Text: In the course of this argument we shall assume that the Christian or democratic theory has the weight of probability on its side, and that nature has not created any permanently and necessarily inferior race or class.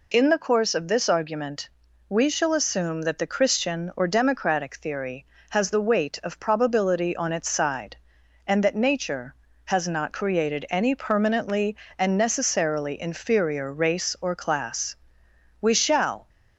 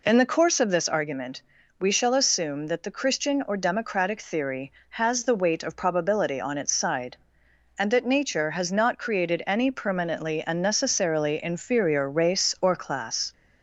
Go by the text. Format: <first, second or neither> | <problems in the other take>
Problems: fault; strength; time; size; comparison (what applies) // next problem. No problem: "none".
second | pauses between "argument" and "we"; slight; at 1.7 s; 0.36 s long; also in the second // goes on to say "We shall"; noticeable; from 15.6 s on; 0.66 s long